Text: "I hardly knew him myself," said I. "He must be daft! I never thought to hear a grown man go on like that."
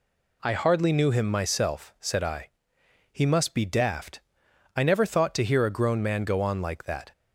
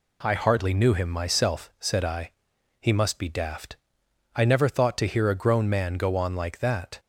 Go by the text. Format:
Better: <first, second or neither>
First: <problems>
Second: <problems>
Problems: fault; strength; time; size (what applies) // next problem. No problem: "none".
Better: neither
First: none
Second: none